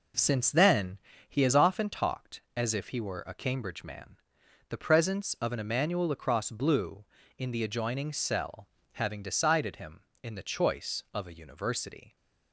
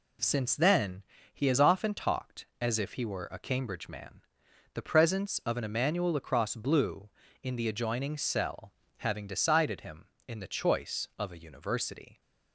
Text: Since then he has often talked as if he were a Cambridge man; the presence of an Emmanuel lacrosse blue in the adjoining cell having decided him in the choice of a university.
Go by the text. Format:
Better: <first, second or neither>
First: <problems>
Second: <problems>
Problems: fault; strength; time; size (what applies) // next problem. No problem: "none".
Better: second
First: starts louder than the rest; noticeable; until 1.7 s; 4.5 dB // pauses between "then" and "he"; slight; at 0.9 s; 0.30 s long // pauses between "cell" and "having"; slight; at 8.6 s; 0.28 s long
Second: pauses between "then" and "he"; slight; at 1.0 s; 0.30 s long // pauses between "cell" and "having"; slight; at 8.6 s; 0.28 s long